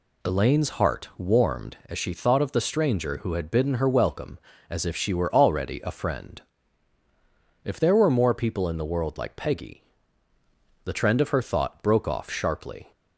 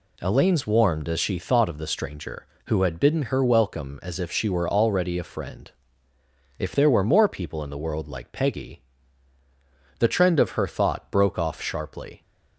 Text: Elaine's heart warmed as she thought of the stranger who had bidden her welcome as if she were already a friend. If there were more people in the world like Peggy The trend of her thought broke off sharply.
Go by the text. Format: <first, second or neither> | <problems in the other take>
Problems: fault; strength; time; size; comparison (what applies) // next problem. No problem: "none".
first | skips "heart"; at 0.6 s // pauses between "Peggy" and "The"; at 8.8 s; 1.1 s long; also in the first